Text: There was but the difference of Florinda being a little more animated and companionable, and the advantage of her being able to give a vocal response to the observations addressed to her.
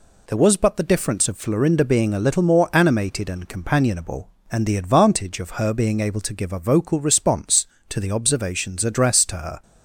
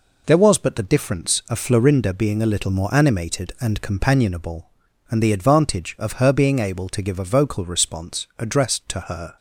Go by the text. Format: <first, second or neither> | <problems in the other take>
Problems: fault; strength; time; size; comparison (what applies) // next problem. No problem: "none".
first | skips "to the observations"; at 8.3 s